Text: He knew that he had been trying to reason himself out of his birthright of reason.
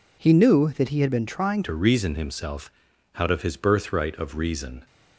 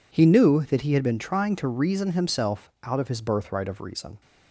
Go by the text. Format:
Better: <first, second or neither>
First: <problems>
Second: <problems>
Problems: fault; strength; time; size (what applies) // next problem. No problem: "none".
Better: second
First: changes voice at "to"; from 1.6 s on; 3.2 s long // pauses between "himself" and "out"; at 2.7 s; 0.44 s long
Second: none